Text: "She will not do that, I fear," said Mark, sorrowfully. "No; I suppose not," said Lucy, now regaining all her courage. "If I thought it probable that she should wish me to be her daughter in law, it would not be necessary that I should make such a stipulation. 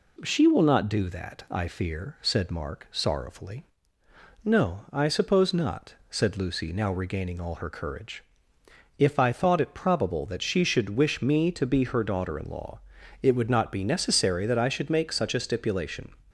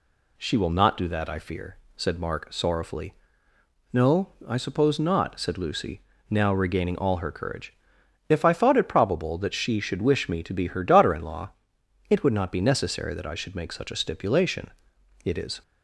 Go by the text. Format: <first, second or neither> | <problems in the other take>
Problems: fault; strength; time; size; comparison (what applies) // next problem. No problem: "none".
first | goes on to say "It is"; slight; from 15.2 s on; 0.38 s long